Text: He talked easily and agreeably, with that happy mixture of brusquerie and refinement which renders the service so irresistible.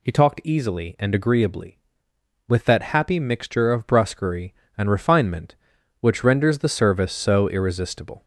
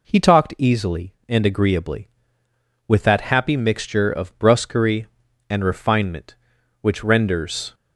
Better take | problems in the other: first | stops before "the service so irresistible"; at 7.7 s

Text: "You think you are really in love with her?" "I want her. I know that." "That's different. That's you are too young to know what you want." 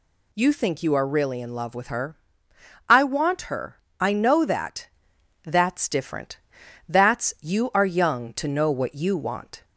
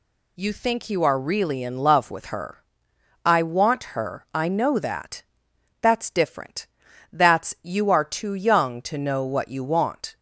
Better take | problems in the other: second | skips "too"; at 7.8 s

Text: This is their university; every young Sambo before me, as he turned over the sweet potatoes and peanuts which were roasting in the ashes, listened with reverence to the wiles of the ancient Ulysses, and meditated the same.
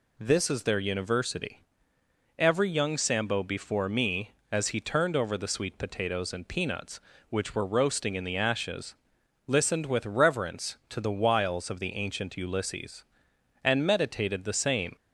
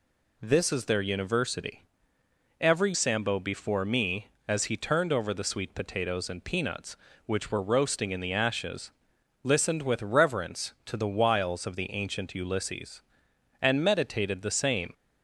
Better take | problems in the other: first | skips "young"; at 2.9 s

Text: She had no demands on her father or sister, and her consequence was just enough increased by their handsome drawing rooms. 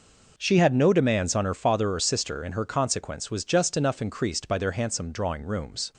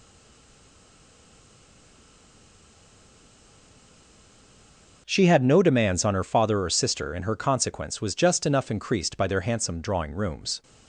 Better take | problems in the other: first | stays silent before the first word; strong; until 5.0 s; 5.0 s long

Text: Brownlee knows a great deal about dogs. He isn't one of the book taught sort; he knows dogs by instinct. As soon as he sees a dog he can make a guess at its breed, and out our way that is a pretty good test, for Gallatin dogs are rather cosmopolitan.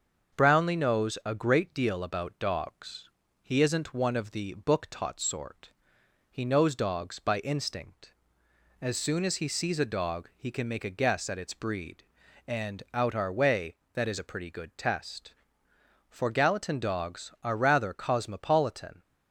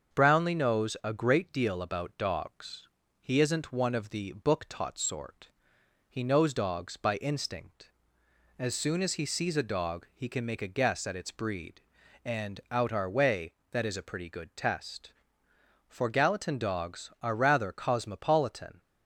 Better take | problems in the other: neither | starts louder than the rest; the same in both

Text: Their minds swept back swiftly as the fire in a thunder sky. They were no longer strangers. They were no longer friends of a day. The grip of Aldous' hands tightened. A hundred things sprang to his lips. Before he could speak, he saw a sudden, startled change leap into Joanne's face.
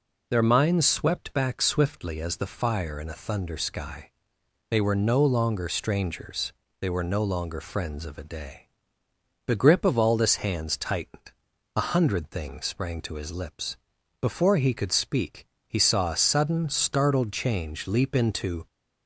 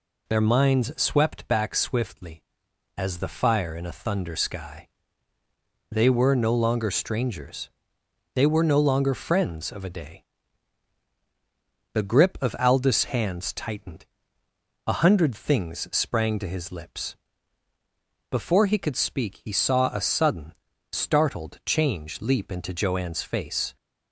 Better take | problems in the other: second | stops before "Joanne's face"; at 18.6 s

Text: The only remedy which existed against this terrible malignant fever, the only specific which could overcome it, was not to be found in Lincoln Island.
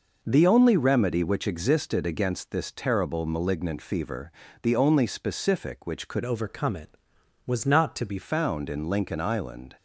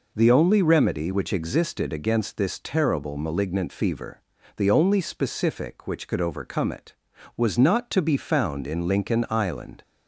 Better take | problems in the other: second | changes voice from "overcome" to "be"; from 6.2 to 8.1 s; 1.9 s long

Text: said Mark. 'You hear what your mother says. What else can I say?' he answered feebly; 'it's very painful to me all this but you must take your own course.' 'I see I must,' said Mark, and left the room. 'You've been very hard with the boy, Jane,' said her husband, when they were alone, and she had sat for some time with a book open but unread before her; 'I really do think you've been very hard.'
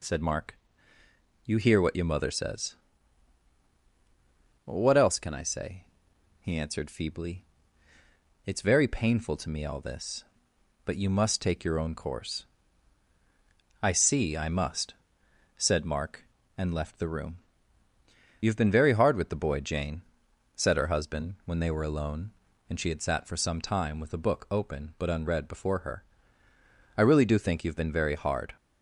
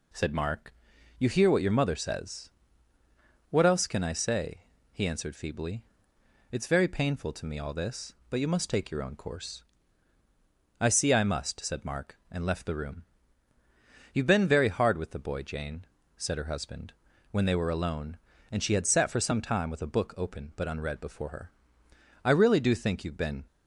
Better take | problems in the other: first | stops before "very hard"; at 23.4 s

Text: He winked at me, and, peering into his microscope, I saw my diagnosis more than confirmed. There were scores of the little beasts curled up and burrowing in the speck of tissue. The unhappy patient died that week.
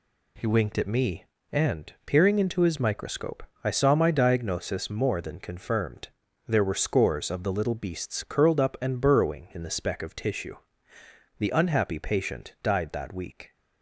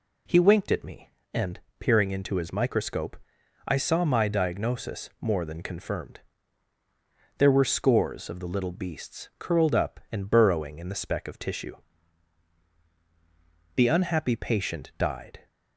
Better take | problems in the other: first | stops before "that week"; at 15.4 s

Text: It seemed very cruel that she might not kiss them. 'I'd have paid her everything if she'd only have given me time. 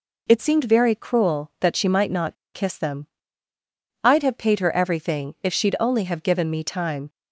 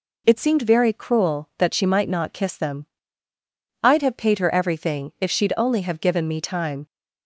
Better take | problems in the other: second | pauses between "not" and "kiss"; slight; at 2.3 s; 0.19 s long

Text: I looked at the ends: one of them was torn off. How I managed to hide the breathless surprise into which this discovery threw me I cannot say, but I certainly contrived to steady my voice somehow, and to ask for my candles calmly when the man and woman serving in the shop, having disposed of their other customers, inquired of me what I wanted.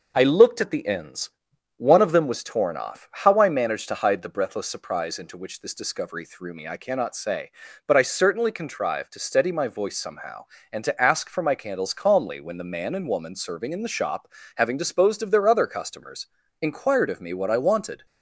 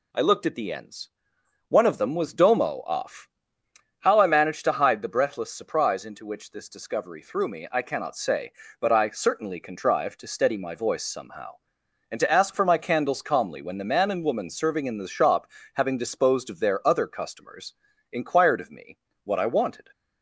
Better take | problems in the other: first | says "domo" for "torn"; at 2.3 s // pauses between "me" and "what"; slight; at 18.9 s; 0.26 s long

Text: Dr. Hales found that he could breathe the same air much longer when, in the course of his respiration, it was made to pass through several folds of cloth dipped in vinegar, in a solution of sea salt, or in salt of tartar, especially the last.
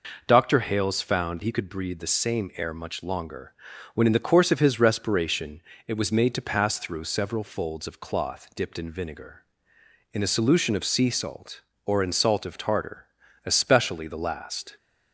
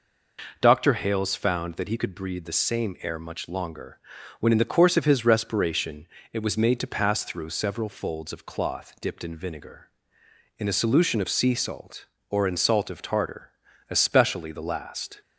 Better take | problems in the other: second | skips "that"; at 1.4 s // pauses between "longer" and "when"; at 3.5 s; 0.40 s long; also in the second

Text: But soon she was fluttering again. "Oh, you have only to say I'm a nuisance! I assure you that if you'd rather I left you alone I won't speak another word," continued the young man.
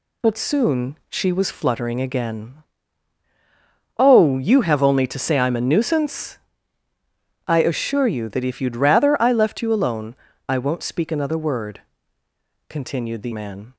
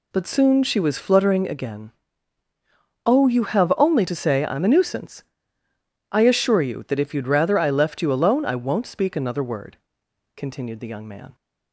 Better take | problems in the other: second | pauses between "alone" and "I"; slight; at 10.1 s; 0.32 s long // skips "young"; at 13.3 s

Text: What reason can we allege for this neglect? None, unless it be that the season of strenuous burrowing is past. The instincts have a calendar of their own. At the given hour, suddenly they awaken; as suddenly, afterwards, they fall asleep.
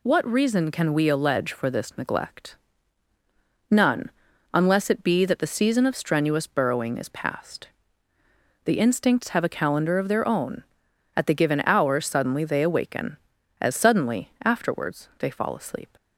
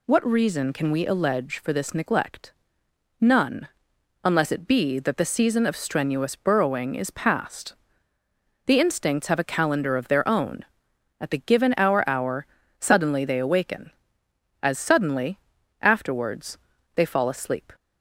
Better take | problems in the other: first | says "hour" twice; at 12.0 s

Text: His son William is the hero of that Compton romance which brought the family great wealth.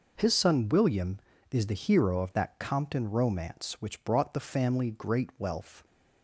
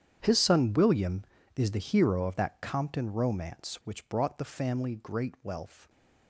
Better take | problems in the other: first | gets quieter; strong; throughout; 17 dB

